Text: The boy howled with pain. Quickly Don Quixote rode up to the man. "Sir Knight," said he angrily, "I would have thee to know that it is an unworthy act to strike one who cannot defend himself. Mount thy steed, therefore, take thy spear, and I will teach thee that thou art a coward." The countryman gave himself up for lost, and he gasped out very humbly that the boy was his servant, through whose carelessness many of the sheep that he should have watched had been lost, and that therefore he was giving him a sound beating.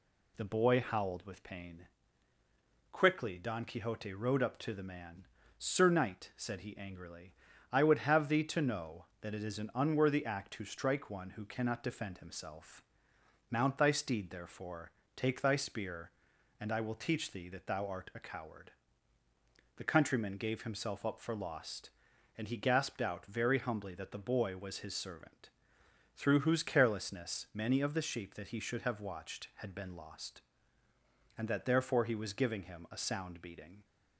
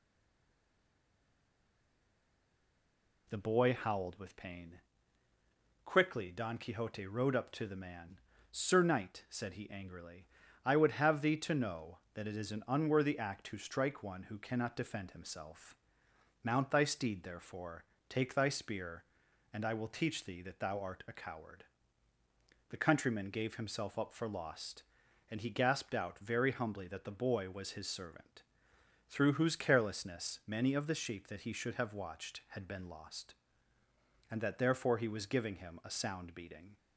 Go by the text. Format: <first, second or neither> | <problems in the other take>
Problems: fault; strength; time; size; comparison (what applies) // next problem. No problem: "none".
first | stays silent before the first word; strong; until 3.2 s; 3.2 s long